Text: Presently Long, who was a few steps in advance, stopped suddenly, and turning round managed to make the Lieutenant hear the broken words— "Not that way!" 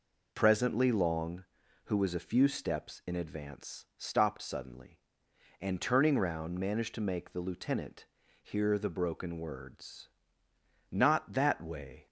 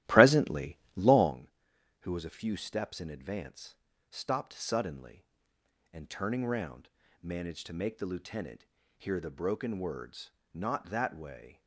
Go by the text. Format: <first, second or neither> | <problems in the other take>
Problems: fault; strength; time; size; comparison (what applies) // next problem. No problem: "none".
first | starts louder than the rest; strong; until 1.4 s; 14.5 dB // pauses between "Presently" and "Long"; slight; at 0.7 s; 0.22 s long // pauses between "round" and "managed"; slight; at 6.8 s; 0.32 s long // pauses between "Lieutenant" and "hear"; slight; at 8.6 s; 0.32 s long; slight in the first